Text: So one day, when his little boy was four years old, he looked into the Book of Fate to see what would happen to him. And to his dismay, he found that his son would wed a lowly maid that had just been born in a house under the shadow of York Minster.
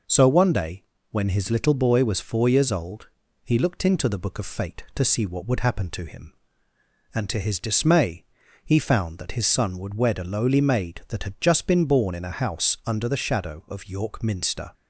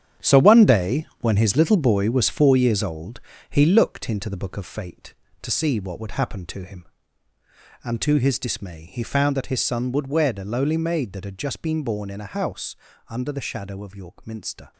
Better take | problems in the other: first | gets quieter; strong; throughout; 11 dB // pauses between "house" and "under"; slight; at 12.7 s; 0.34 s long

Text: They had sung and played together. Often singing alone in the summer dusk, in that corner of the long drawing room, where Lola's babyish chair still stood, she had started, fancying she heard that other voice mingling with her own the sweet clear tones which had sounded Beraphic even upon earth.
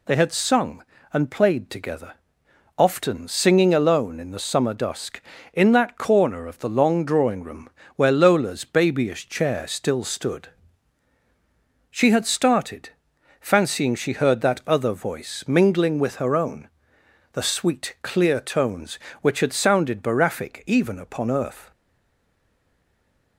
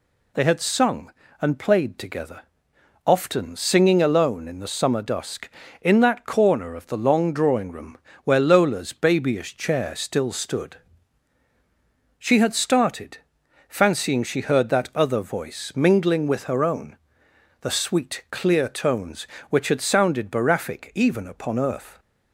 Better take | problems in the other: second | pauses between "own" and "the"; noticeable; at 16.6 s; 0.64 s long; noticeable in the second // stays silent after the last word; noticeable; from 21.7 s on; 1.6 s long

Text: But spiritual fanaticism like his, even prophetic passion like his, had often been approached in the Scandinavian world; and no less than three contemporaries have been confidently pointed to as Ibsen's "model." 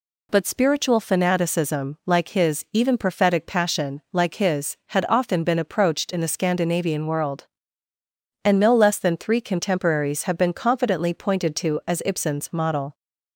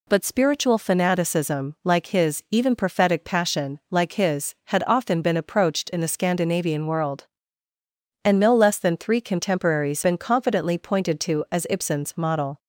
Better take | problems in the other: first | skips "have"; at 10.0 s

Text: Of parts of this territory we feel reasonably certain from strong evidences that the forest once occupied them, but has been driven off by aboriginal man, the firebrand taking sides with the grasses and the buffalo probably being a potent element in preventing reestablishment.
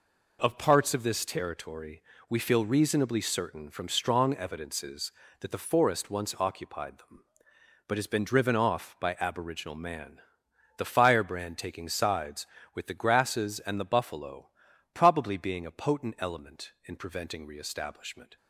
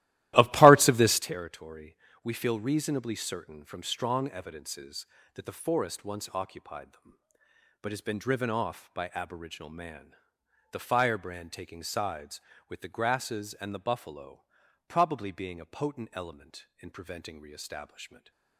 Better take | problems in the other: first | starts louder than the rest; strong; until 1.3 s; 16 dB // pauses between "territory" and "we"; slight; at 1.9 s; 0.28 s long; slight in the first // pauses between "buffalo" and "probably"; noticeable; at 14.4 s; 0.46 s long; noticeable in the first // stays silent after the last word; slight; from 18.0 s on; 0.5 s long

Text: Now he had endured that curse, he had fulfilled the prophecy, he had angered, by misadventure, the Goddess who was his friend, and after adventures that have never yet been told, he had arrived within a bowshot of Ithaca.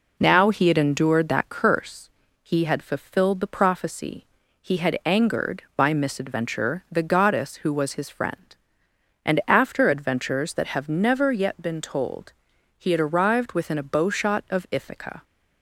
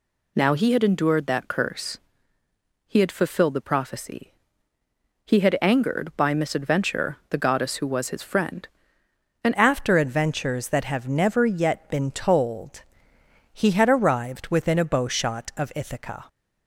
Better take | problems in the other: first | changes voice at "after"; from 9.5 s on; 6.7 s long

